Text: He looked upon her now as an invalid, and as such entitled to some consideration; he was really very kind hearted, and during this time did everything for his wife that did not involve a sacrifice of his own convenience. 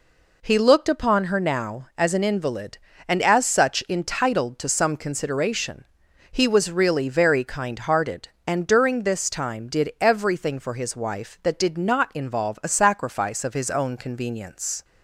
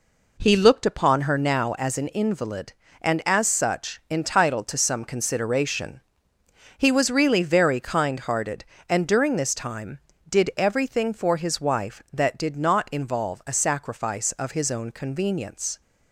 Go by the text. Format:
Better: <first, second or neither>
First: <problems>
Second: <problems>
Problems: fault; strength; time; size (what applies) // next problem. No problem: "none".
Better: neither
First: none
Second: none